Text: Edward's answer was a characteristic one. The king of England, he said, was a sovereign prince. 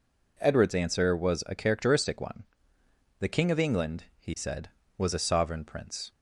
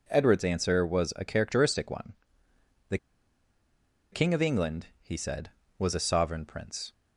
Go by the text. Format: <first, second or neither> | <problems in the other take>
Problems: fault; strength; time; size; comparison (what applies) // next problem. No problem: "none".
first | pauses between "The" and "king"; at 2.9 s; 1.1 s long